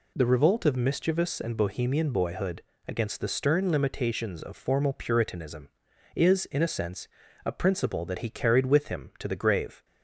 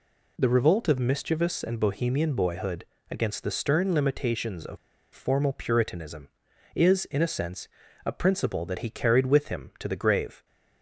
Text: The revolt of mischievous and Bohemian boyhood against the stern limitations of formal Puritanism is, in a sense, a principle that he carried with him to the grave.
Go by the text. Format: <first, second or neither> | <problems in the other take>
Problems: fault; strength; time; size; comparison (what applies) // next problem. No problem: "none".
first | pauses between "boyhood" and "against"; slight; at 2.8 s; 0.26 s long; slight in the first // pauses between "of" and "formal"; at 4.7 s; 0.37 s long